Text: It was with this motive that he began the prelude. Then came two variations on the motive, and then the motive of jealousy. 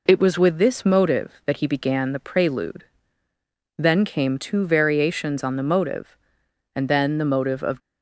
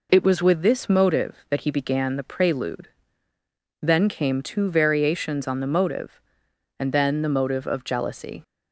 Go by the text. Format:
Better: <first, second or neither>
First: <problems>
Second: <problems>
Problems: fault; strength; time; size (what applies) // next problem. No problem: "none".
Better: second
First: stops before "jealousy"; at 7.8 s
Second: none